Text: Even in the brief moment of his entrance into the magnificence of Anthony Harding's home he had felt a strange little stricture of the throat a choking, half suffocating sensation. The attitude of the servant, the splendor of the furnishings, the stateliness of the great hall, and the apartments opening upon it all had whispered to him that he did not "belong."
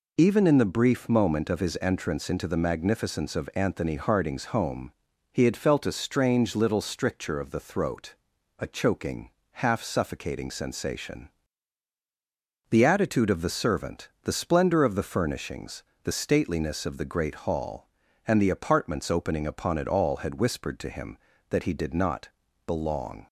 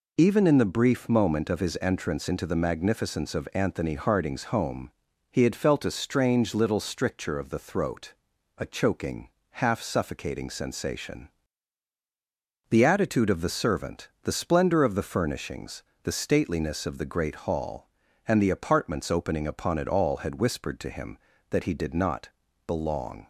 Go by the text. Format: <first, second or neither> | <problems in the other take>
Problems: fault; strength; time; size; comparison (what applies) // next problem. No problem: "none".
neither | pauses between "home" and "he"; the same in both // pauses between "throat" and "a"; the same in both // pauses between "not" and "belong"; the same in both